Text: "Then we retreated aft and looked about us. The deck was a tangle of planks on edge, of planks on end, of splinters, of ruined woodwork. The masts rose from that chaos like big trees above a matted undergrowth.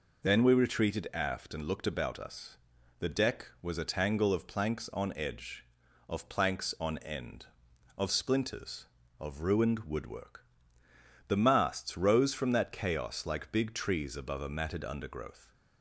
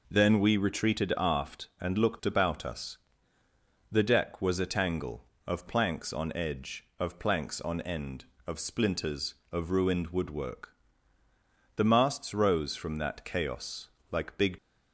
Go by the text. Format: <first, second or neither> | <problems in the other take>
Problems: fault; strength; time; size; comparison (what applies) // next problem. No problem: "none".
first | pauses between "chaos" and "like"; slight; at 13.8 s; 0.22 s long // stops before "trees above a matted undergrowth"; at 14.5 s